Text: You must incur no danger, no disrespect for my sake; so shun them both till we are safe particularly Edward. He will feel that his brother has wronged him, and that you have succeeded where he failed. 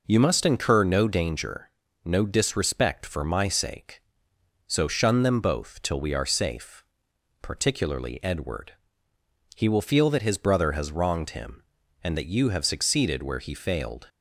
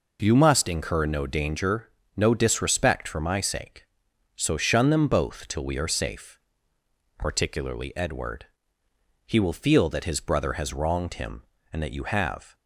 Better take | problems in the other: first | pauses between "safe" and "particularly"; noticeable; at 6.3 s; 0.78 s long; noticeable in the first // stops before "succeeded where he failed"; at 12.5 s

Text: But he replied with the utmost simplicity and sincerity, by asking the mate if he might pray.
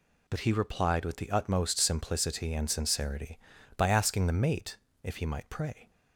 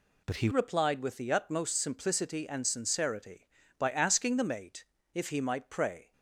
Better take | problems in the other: first | changes voice at "replied"; from 0.5 s on; 5.6 s long // pauses between "mate" and "if"; slight; at 4.8 s; 0.30 s long; slight in the first

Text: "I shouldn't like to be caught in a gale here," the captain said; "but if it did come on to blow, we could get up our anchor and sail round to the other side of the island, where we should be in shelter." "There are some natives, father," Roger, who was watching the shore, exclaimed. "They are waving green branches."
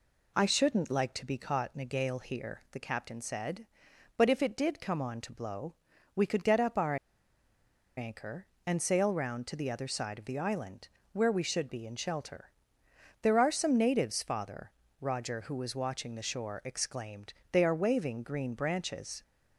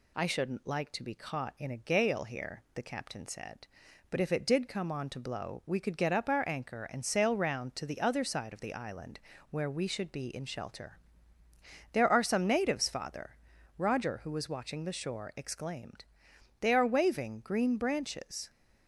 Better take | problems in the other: second | pauses between "our" and "anchor"; at 6.9 s; 1.0 s long

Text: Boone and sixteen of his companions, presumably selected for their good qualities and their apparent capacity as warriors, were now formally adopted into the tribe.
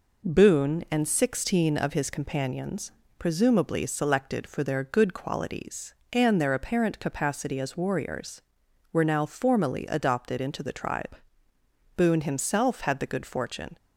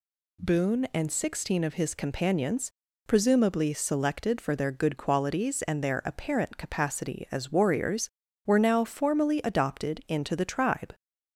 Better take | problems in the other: second | goes on to say "Boone himself had the good fortune"; strong; from 11.9 s on; 1.8 s long

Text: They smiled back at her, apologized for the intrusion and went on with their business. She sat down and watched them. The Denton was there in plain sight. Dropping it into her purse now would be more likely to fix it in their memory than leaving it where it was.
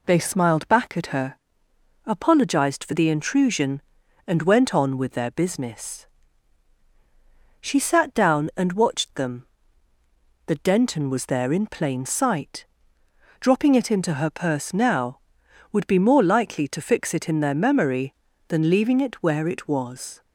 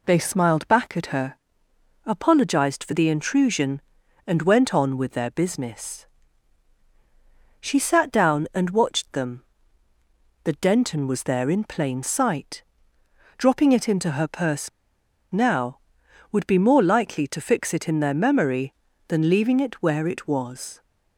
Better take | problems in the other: first | pauses between "purse" and "now"; noticeable; at 14.6 s; 0.62 s long

